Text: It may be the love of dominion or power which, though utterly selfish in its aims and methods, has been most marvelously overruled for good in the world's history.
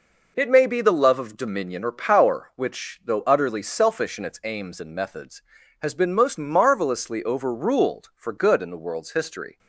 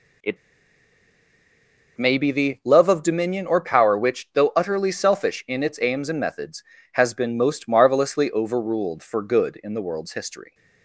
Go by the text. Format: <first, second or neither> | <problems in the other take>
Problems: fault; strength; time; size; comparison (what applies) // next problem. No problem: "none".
first | pauses between "It" and "may"; strong; at 0.3 s; 1.6 s long